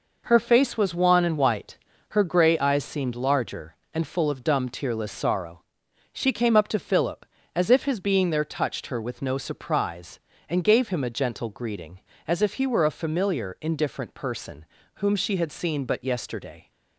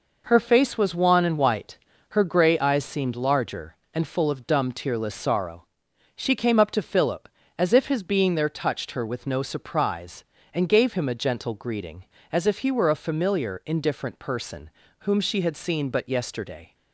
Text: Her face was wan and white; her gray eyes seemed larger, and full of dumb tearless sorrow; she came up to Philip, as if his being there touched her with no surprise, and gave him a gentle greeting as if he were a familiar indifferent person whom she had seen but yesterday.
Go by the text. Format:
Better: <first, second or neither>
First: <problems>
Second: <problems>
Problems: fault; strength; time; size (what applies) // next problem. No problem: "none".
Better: neither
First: pauses between "person" and "whom"; slight; at 14.6 s; 0.36 s long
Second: pauses between "person" and "whom"; slight; at 14.6 s; 0.36 s long